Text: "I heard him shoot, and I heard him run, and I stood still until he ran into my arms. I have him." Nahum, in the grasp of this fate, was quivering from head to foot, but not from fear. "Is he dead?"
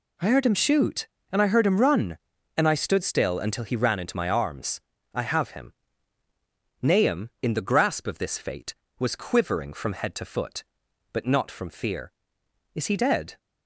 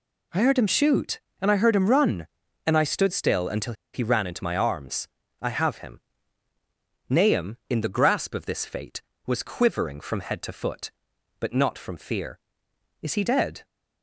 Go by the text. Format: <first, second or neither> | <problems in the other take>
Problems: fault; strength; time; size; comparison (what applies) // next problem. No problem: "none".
first | pauses between "until" and "he"; slight; at 3.7 s; 0.20 s long